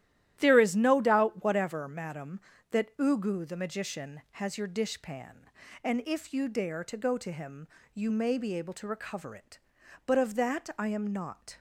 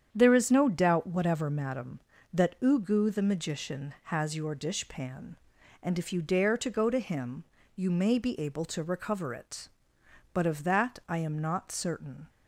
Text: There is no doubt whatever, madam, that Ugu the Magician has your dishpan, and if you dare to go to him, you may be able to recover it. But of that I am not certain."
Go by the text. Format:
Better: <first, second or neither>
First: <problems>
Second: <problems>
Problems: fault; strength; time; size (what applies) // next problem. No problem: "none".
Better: second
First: starts louder than the rest; strong; until 1.3 s; 12.5 dB // stops before "certain"; at 11.5 s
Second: starts louder than the rest; strong; until 1.1 s; 8.5 dB